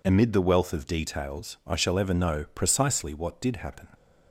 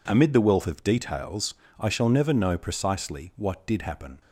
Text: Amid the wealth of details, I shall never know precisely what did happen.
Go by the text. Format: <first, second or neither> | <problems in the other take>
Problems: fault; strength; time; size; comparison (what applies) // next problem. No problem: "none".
second | says "ever" for "never"; at 1.9 s